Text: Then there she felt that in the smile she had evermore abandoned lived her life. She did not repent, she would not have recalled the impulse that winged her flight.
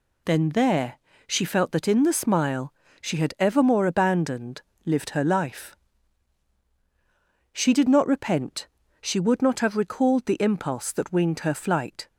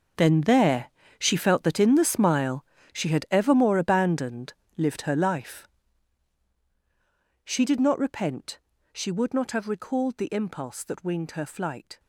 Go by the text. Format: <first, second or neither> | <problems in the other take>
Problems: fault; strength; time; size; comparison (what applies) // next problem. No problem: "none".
first | gets quieter; strong; throughout; 15 dB // pauses between "there" and "she"; slight; at 0.8 s; 0.30 s long; slight in the first // pauses between "smile" and "she"; slight; at 2.6 s; 0.30 s long; slight in the first // pauses between "abandoned" and "lived"; slight; at 4.5 s; 0.24 s long; slight in the first